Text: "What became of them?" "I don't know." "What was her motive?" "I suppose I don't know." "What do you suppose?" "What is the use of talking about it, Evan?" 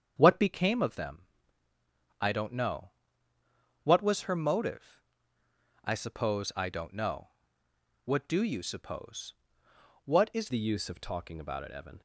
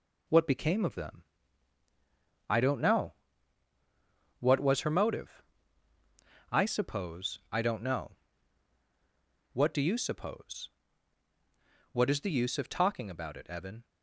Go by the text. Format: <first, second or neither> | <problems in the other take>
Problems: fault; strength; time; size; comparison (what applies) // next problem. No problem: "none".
second | starts louder than the rest; strong; until 1.1 s; 7.5 dB // changes voice at "the"; from 10.5 s on; 1.5 s long